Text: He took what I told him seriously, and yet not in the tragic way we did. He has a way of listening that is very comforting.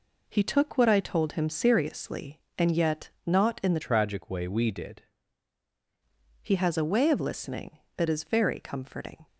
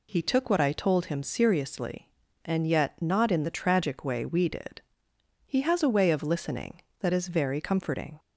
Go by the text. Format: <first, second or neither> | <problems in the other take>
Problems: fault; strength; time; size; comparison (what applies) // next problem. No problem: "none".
second | pauses between "yet" and "not"; slight; at 3.0 s; 0.16 s long // changes voice from "tragic" to "did"; from 3.8 to 5.0 s; 1.2 s long